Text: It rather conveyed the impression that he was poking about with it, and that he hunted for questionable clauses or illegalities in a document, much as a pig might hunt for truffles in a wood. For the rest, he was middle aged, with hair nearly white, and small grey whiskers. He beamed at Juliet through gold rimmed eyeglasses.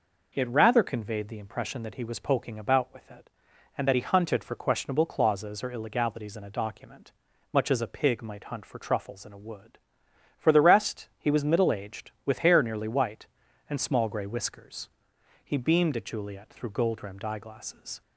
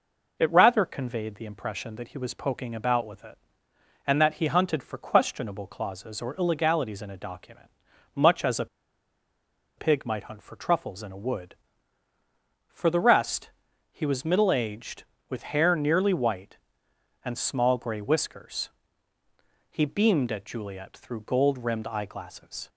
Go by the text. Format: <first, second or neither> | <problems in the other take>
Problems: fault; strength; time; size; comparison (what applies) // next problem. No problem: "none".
first | pauses between "a" and "pig"; at 8.6 s; 1.1 s long